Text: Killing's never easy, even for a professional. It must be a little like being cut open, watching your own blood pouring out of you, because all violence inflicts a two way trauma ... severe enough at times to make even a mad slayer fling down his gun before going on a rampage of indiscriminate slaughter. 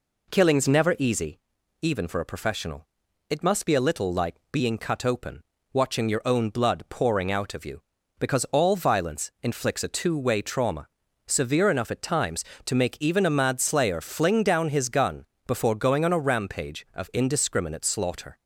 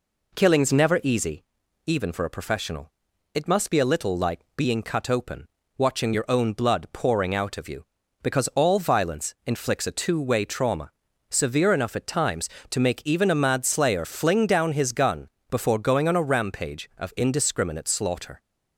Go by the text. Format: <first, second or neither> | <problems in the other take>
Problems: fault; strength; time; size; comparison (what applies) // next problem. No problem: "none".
neither | pauses between "like" and "being"; slight; the same in both // pauses between "gun" and "before"; slight; the same in both